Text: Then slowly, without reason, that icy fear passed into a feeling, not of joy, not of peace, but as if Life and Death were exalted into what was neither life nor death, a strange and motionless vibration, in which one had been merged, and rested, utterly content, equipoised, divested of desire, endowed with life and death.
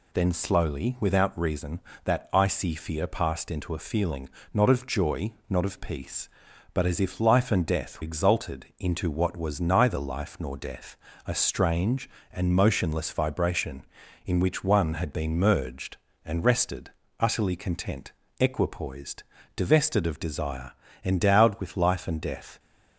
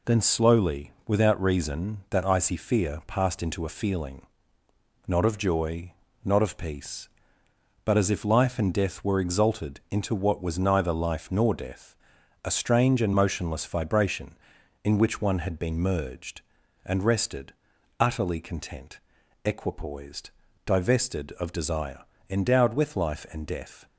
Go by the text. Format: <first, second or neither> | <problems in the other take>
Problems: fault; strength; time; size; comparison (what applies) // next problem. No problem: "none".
second | skips "were"; at 8.0 s